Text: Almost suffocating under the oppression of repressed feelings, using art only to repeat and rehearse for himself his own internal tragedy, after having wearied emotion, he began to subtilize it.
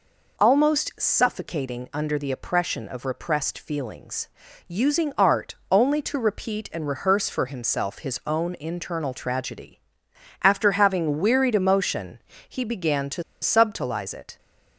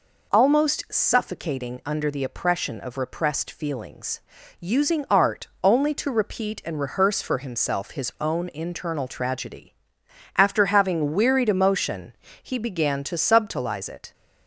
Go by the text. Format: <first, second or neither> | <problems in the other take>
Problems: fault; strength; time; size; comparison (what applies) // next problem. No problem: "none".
second | pauses between "art" and "only"; slight; at 5.5 s; 0.16 s long; slight in the second // pauses between "to" and "subtilize"; slight; at 13.2 s; 0.19 s long